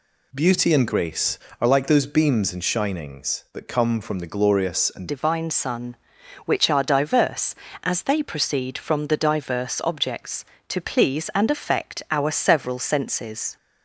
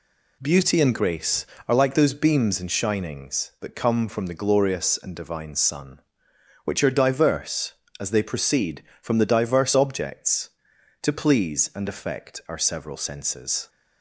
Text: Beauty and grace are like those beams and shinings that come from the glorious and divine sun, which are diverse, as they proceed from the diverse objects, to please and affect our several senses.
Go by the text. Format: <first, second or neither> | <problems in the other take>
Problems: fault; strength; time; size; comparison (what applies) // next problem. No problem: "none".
second | changes voice at "divine"; from 5.0 s on; 8.5 s long